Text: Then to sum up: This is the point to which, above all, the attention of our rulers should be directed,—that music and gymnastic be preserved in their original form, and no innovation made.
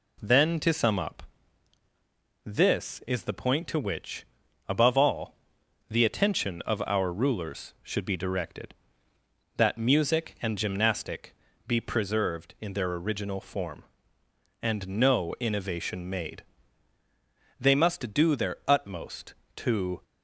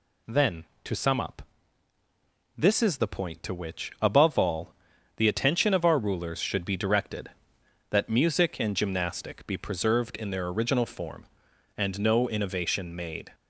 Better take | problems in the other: second | pauses between "gymnastic" and "be"; slight; at 11.3 s; 0.32 s long // goes on to say "They must do their utmost to"; strong; from 17.5 s on; 2.4 s long

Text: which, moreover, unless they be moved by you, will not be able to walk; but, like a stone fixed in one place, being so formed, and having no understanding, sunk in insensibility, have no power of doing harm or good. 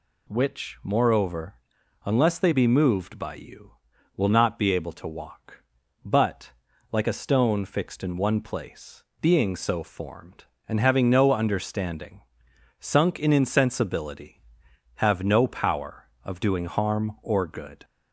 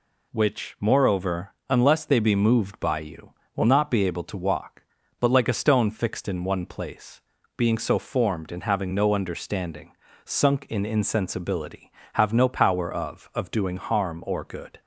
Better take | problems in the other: first | says "of" twice; at 13.3 s

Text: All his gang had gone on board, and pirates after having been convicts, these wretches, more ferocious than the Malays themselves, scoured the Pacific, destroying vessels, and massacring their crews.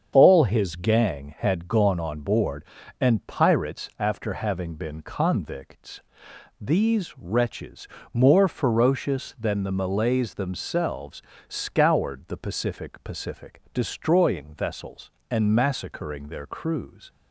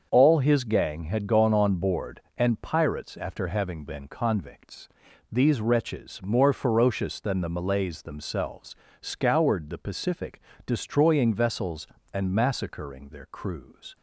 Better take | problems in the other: second | starts louder than the rest; strong; until 1.1 s; 7.5 dB; also in the second // says "Pacific" twice; at 13.0 s

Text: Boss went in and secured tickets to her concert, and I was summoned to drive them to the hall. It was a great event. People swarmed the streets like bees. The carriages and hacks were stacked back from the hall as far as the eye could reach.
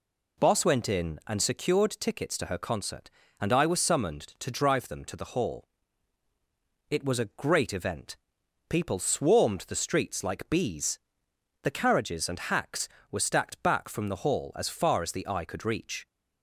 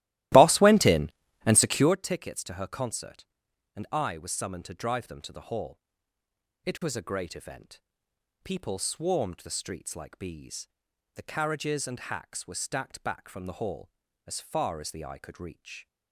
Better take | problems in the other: first | starts louder than the rest; strong; until 2.0 s; 16.5 dB

